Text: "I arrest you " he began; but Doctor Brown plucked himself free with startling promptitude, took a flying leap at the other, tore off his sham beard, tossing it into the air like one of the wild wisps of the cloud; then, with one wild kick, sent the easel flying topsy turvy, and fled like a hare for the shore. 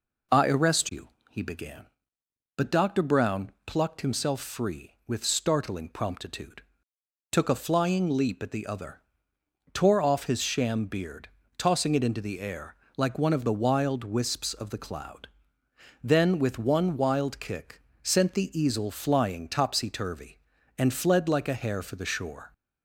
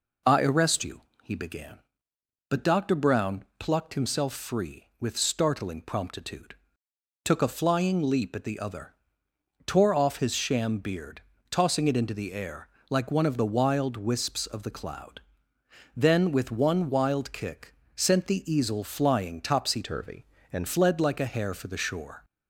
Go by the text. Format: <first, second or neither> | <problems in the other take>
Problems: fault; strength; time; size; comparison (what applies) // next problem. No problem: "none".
first | pauses between "Brown" and "plucked"; slight; at 3.4 s; 0.16 s long; slight in the first // pauses between "air" and "like"; slight; at 12.6 s; 0.20 s long; slight in the first // changes voice from "turvy" to "and"; from 19.8 to 20.6 s; 0.8 s long